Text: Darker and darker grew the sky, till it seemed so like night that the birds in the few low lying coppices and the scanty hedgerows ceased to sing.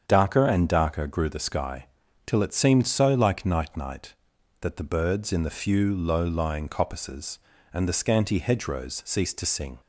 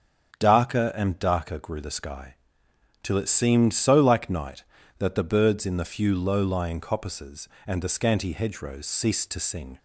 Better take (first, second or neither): second